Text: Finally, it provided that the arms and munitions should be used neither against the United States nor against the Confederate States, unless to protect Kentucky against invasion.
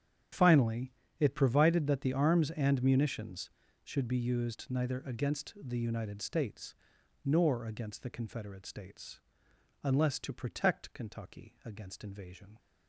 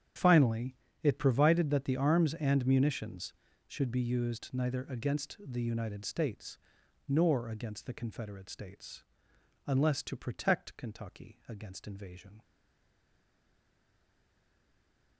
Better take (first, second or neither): first